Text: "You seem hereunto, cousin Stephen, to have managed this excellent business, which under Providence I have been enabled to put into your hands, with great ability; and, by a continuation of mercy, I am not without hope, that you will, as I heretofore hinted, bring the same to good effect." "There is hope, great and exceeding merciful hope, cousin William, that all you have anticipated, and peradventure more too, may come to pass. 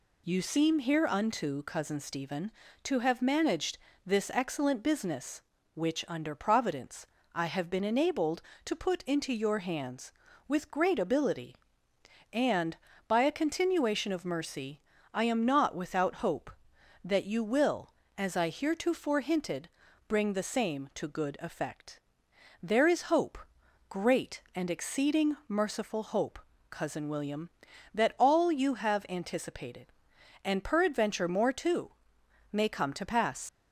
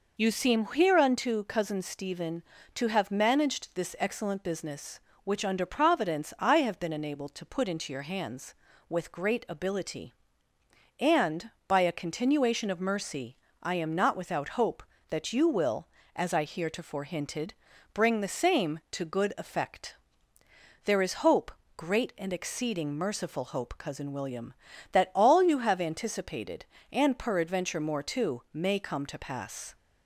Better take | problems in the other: second | pauses between "managed" and "this"; slight; at 3.7 s; 0.30 s long // pauses between "Providence" and "I"; slight; at 7.0 s; 0.30 s long // leaves "pass" unfinished; at 33.4 s; 85 ms

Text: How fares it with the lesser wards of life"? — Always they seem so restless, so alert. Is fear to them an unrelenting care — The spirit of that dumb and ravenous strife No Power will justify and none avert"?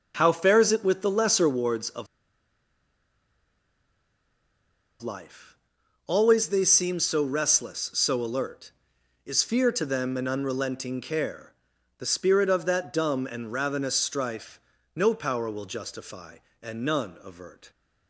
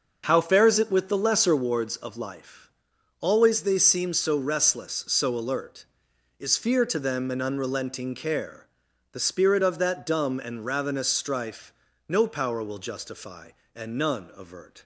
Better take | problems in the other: second | pauses between "of" and "life"; strong; at 2.0 s; 2.9 s long // pauses between "strife" and "No"; slight; at 14.5 s; 0.36 s long; slight in the second

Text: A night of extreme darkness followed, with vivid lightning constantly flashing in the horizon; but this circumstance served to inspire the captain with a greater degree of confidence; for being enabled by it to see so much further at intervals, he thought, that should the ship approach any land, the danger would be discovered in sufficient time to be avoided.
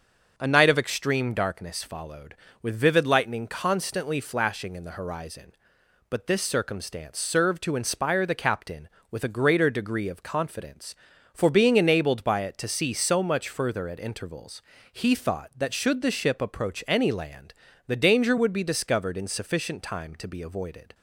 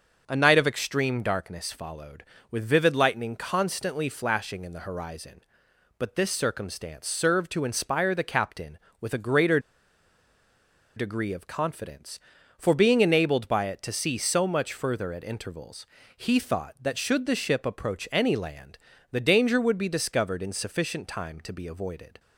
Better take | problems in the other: first | starts louder than the rest; until 1.2 s; 6.5 dB; also in the first // pauses between "greater" and "degree"; strong; at 9.5 s; 1.3 s long

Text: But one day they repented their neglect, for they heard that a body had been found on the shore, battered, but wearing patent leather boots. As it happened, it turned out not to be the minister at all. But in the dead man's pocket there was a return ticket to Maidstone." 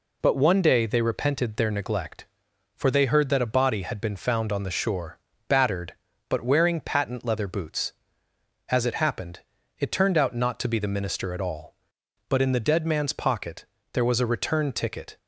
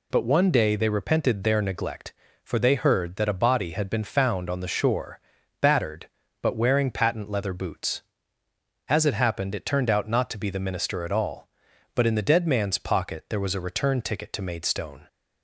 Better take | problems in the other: second | pauses between "pocket" and "there"; slight; at 13.6 s; 0.28 s long // stops before "to Maidstone"; at 15.1 s

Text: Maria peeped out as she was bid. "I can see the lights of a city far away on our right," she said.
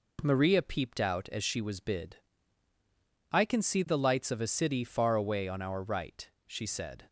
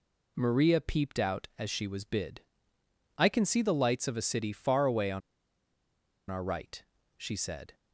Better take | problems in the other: first | pauses between "on" and "our"; at 5.2 s; 1.0 s long

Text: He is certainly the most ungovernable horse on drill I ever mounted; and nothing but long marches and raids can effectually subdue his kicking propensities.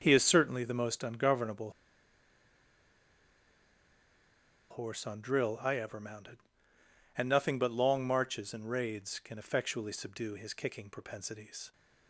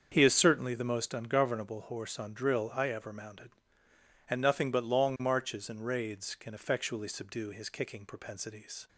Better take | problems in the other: second | starts louder than the rest; until 1.0 s; 6.5 dB; also in the second // pauses between "ungovernable" and "horse"; strong; at 1.7 s; 3.0 s long

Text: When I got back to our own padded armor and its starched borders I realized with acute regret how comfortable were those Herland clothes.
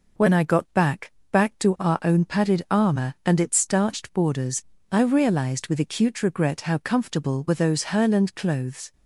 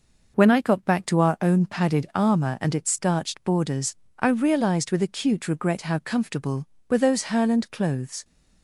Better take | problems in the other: second | says "back" twice; at 1.3 s // pauses between "borders" and "I"; slight; at 4.6 s; 0.30 s long; slight in the second

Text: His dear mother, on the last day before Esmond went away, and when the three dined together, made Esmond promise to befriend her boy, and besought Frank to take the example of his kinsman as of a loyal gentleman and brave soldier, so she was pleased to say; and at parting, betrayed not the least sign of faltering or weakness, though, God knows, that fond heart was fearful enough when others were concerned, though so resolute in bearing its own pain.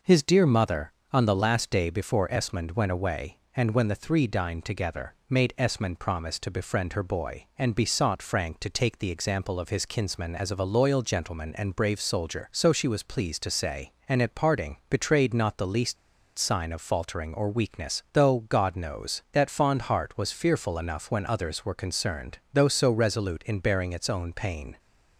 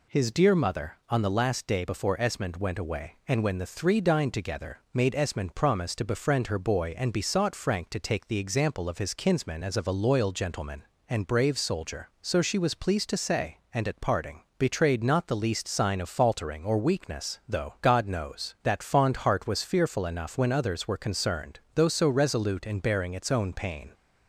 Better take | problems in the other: second | pauses between "least" and "sign"; at 15.9 s; 0.41 s long

